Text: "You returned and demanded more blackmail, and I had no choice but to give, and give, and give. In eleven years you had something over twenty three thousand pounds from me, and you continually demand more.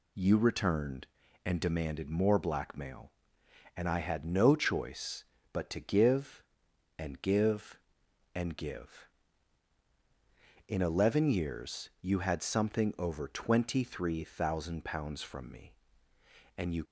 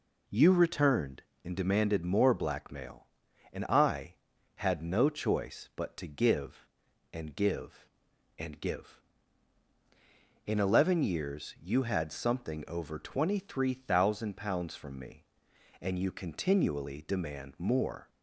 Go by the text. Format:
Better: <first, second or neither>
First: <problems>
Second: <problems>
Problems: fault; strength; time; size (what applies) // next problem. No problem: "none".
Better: second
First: stops before "continually demand more"; at 16.8 s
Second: none